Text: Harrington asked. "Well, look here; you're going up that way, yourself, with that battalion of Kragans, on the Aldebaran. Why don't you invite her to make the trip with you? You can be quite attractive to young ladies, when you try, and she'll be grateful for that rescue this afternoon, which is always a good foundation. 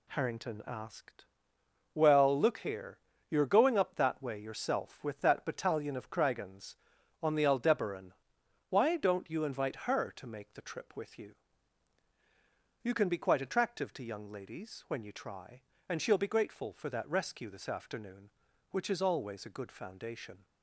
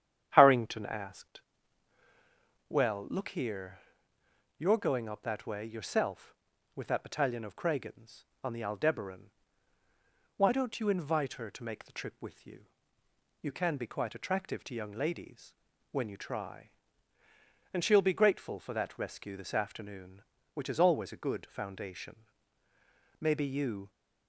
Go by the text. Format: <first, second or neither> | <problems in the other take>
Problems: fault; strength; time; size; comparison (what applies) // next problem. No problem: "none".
first | starts louder than the rest; strong; until 1.3 s; 9.5 dB // goes on to say "Maybe you"; noticeable; from 23.1 s on; 0.70 s long